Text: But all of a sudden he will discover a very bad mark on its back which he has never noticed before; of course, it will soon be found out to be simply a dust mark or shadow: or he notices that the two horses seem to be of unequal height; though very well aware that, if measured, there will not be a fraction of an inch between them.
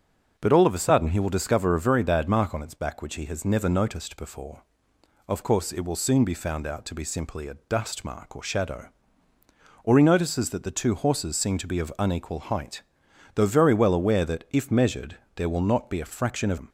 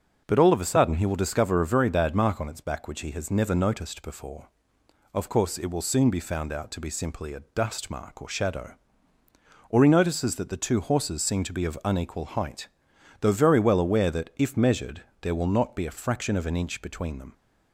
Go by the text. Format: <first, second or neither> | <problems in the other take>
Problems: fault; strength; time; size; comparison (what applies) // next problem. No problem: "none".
second | starts louder than the rest; until 1.3 s; 6.5 dB // skips "an inch between"; at 16.5 s